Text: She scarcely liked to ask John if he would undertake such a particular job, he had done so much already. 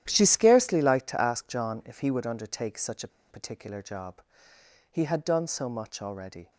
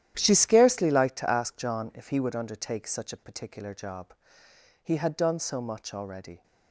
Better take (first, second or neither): second